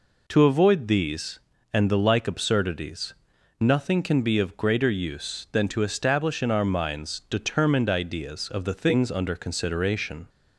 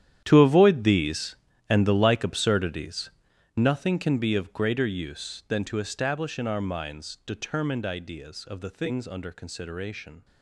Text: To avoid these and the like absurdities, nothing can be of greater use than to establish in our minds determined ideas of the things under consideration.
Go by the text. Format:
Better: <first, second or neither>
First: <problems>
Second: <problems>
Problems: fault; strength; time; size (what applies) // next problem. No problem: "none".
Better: first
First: none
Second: gets quieter; strong; throughout; 16 dB